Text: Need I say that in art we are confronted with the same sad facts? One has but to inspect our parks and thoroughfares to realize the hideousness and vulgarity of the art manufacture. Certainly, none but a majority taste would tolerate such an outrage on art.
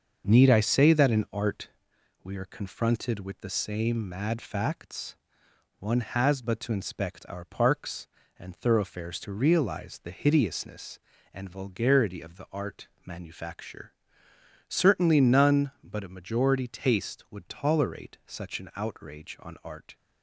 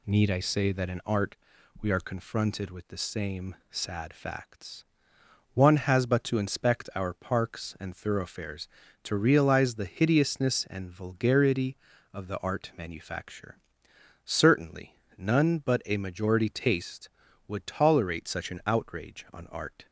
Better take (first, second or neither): second